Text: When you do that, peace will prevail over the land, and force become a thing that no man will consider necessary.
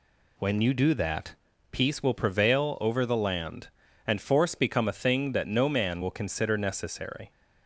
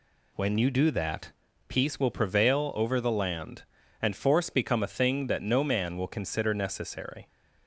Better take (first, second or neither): neither